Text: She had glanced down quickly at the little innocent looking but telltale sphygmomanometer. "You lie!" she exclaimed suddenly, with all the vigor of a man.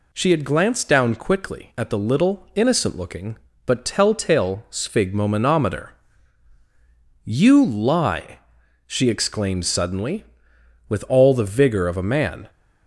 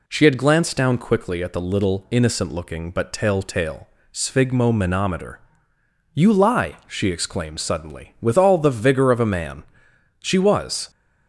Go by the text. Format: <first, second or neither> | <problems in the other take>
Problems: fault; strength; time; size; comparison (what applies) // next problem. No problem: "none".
first | pauses between "telltale" and "sphygmomanometer"; slight; at 3.8 s; 0.26 s long // goes on to say "She was"; noticeable; from 10.1 s on; 0.70 s long